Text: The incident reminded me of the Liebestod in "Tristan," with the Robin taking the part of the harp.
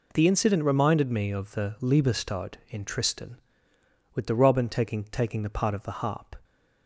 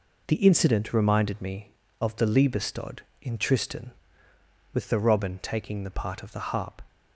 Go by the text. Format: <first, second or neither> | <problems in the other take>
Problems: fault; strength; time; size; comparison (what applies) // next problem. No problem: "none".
second | says "taking" twice; at 5.0 s